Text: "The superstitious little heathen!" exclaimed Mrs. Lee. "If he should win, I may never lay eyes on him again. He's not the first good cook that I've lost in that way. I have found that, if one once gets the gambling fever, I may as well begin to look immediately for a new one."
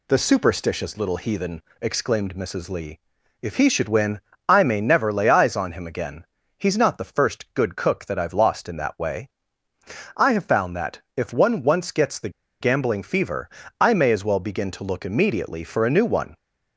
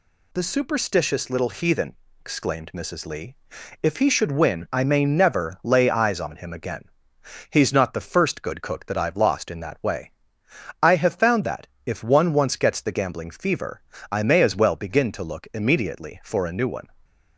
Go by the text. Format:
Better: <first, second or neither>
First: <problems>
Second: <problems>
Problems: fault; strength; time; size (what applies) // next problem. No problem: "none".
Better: second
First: pauses between "the" and "gambling"; slight; at 12.2 s; 0.31 s long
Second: none